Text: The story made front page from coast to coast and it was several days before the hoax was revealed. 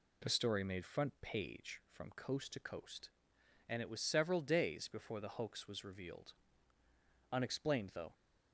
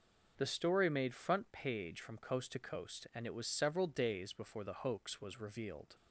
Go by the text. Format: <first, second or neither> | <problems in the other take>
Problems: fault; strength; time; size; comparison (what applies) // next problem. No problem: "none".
second | goes on to say "Unexplained though"; noticeable; from 7.3 s on; 0.80 s long